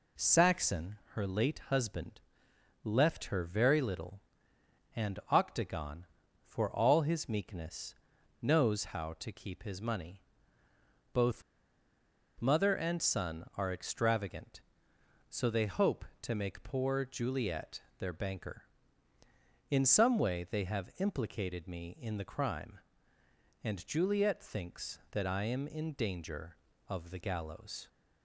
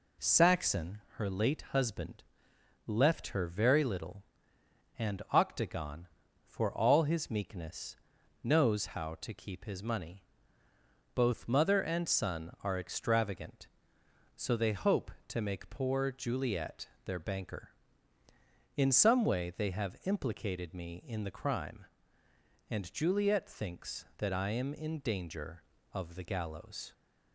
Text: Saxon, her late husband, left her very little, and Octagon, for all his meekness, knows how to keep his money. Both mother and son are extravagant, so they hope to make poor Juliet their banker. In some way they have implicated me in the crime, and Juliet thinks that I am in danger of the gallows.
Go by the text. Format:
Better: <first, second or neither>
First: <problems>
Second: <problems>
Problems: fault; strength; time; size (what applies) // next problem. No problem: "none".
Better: second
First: pauses between "Both" and "mother"; noticeable; at 11.4 s; 0.97 s long // pauses between "Juliet" and "their"; slight; at 17.8 s; 0.16 s long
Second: pauses between "Juliet" and "their"; slight; at 16.8 s; 0.16 s long